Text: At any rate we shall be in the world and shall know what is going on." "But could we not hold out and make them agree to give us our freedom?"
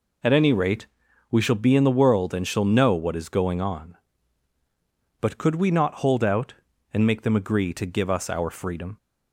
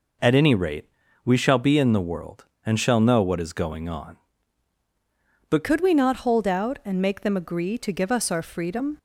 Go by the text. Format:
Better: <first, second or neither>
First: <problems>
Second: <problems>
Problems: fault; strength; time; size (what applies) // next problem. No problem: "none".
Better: first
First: pauses between "rate" and "we"; at 0.8 s; 0.42 s long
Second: pauses between "rate" and "we"; slight; at 0.8 s; 0.36 s long // changes voice at "could"; from 5.6 s on; 3.3 s long